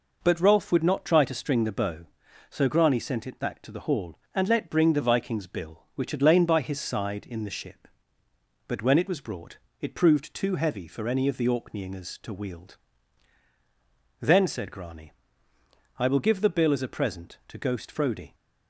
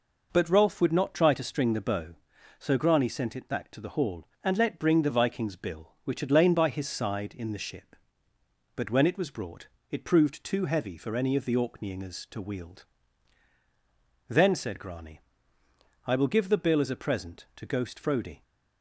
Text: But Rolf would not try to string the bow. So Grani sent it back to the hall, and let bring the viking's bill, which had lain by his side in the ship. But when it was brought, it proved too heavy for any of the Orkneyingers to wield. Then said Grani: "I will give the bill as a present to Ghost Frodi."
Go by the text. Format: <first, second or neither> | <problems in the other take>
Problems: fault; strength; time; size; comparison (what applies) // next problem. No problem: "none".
neither | none